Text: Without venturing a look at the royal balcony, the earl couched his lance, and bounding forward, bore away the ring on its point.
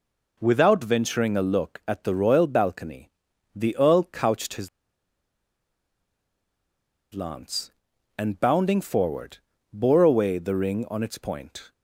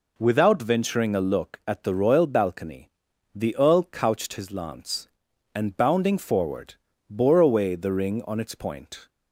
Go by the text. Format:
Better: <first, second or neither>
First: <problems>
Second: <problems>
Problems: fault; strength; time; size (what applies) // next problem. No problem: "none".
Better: second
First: pauses between "his" and "lance"; strong; at 4.6 s; 2.4 s long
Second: none